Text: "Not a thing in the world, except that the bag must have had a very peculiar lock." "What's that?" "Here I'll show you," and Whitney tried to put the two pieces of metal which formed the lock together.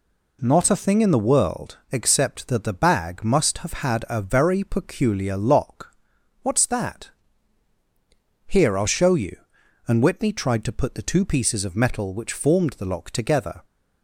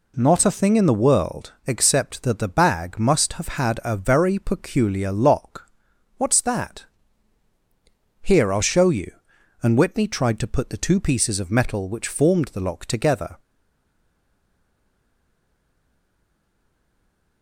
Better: first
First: none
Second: stays silent after the last word; strong; from 13.3 s on; 4.1 s long

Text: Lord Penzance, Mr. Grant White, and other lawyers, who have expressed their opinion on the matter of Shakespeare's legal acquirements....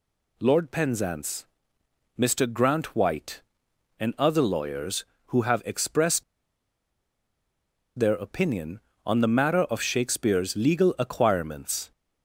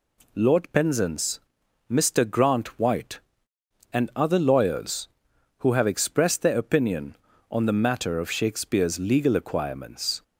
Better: second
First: pauses between "expressed" and "their"; strong; at 6.2 s; 1.7 s long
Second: none

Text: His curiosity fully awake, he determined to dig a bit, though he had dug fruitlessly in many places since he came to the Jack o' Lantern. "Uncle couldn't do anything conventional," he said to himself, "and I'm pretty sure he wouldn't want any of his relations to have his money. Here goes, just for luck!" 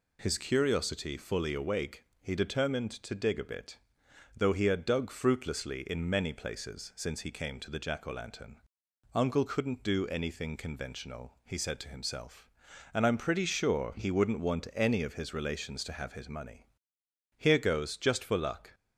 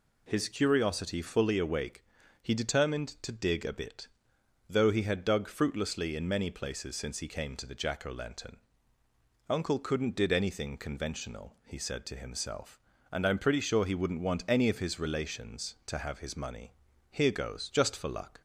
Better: first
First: none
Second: says "did" for "do"; at 10.1 s

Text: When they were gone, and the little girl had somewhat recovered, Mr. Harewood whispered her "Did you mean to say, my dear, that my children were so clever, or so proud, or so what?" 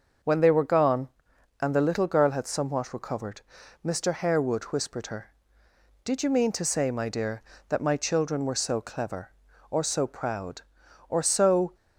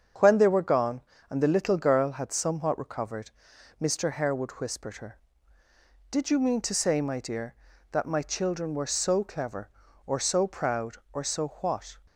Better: second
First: starts louder than the rest; until 1.7 s; 6 dB // stops before "what"; at 11.7 s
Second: starts louder than the rest; strong; until 1.4 s; 7 dB

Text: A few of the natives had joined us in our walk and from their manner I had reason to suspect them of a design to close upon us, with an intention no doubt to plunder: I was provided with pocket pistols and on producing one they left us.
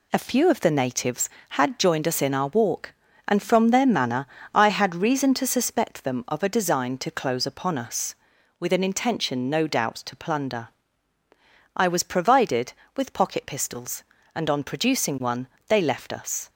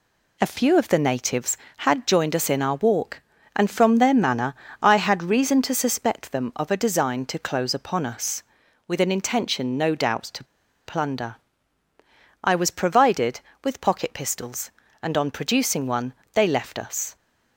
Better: first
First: pauses between "manner" and "I"; slight; at 4.2 s; 0.28 s long // pauses between "one" and "they"; slight; at 15.4 s; 0.18 s long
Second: pauses between "manner" and "I"; slight; at 4.5 s; 0.28 s long // pauses between "to" and "plunder"; at 10.4 s; 0.42 s long // pauses between "one" and "they"; slight; at 16.1 s; 0.18 s long

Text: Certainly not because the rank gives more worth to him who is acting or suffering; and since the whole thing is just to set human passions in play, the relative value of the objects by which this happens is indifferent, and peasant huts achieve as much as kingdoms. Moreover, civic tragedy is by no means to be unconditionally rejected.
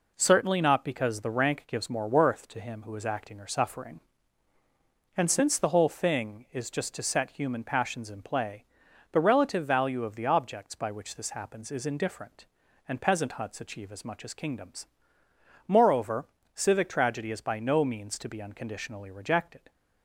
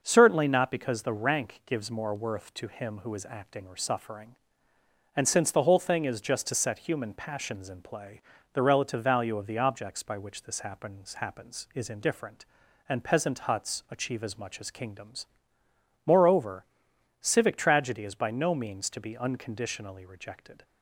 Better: first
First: none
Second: starts louder than the rest; noticeable; until 1.0 s; 6 dB // says "happens" twice; at 11.1 s

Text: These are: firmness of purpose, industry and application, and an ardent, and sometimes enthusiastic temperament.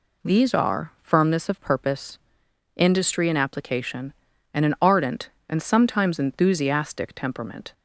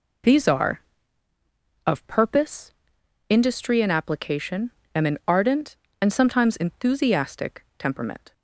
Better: first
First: none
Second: skips "firmness"; at 1.3 s

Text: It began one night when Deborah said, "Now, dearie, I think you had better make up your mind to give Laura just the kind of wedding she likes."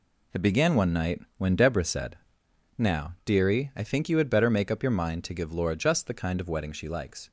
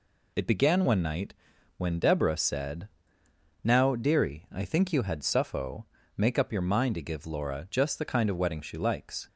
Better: first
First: pauses between "night" and "when"; slight; at 1.2 s; 0.18 s long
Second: pauses between "night" and "when"; at 1.3 s; 0.42 s long // says "suffo" for "better"; at 5.2 s

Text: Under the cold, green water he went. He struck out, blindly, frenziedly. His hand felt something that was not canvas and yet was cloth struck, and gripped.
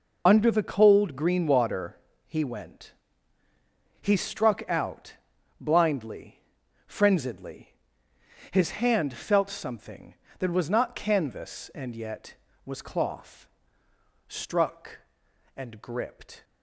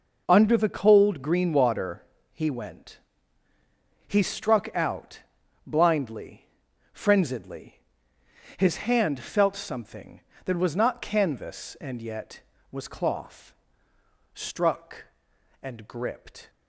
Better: second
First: loses the start of "Under"; at 0.2 s; 40 ms // pauses between "water" and "he"; slight; at 1.9 s; 0.30 s long // pauses between "cloth" and "struck"; noticeable; at 13.4 s; 0.82 s long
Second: pauses between "water" and "he"; slight; at 2.0 s; 0.30 s long // pauses between "cloth" and "struck"; noticeable; at 13.5 s; 0.82 s long

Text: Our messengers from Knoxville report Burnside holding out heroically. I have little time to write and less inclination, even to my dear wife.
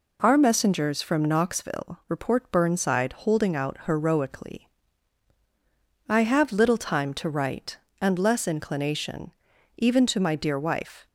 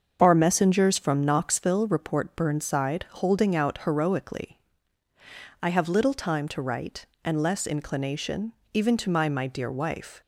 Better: first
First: none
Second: starts louder than the rest; until 1.2 s; 6.5 dB // says "my" twice; at 9.2 s

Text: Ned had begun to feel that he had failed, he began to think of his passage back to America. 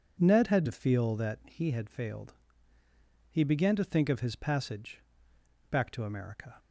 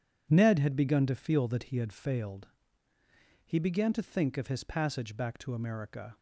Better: second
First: skips "begun"; at 0.6 s // pauses between "passage" and "back"; noticeable; at 4.9 s; 0.70 s long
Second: none

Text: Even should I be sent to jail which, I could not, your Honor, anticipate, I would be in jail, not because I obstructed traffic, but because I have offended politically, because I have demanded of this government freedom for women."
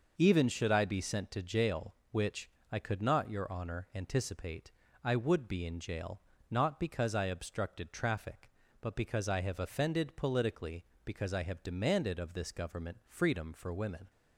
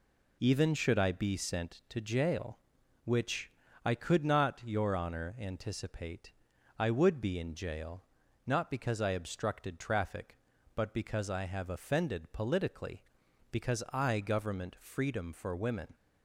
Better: first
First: none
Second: skips "have demanded of this"; at 14.2 s

